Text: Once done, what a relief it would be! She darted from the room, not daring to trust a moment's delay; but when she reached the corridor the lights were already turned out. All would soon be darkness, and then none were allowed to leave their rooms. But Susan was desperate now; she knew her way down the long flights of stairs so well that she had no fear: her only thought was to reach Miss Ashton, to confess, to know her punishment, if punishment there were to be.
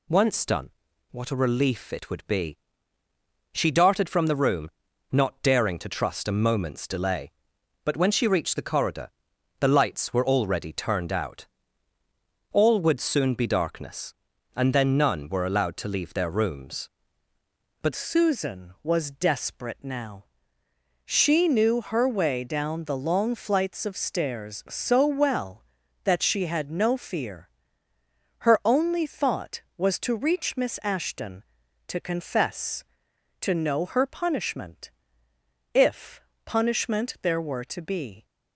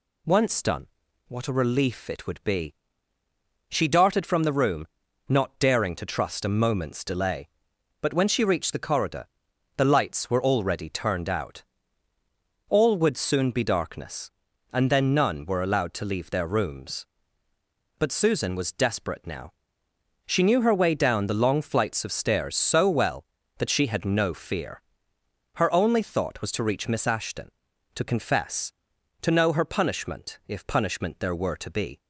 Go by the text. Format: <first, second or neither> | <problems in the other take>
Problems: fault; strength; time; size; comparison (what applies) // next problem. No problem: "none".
second | pauses between "corridor" and "the"; noticeable; at 9.0 s; 0.50 s long; noticeable in the second // changes voice at "Susan"; from 17.9 s on; 20.3 s long // pauses between "if" and "punishment"; slight; at 36.2 s; 0.24 s long